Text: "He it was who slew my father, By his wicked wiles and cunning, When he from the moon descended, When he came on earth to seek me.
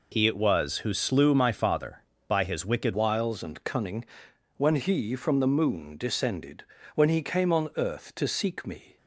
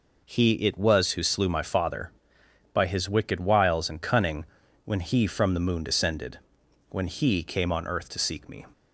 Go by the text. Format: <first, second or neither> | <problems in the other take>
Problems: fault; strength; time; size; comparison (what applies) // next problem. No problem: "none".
second | changes voice at "wiles"; from 2.9 s on; 6.0 s long